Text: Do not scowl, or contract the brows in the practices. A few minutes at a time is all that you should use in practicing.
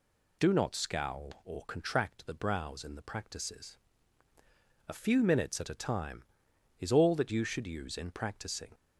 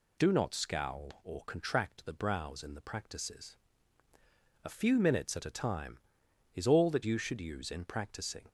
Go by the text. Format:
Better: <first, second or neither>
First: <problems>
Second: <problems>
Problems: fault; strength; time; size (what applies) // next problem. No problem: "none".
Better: neither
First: none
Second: none